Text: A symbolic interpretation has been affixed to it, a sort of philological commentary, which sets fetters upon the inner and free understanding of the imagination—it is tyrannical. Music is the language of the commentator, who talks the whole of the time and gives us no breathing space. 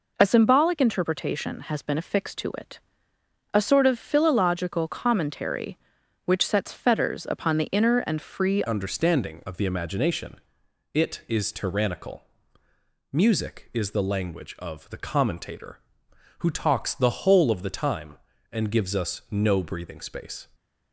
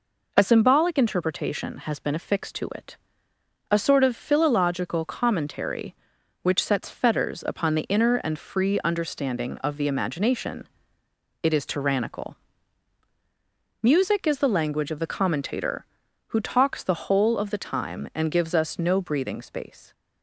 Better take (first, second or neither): second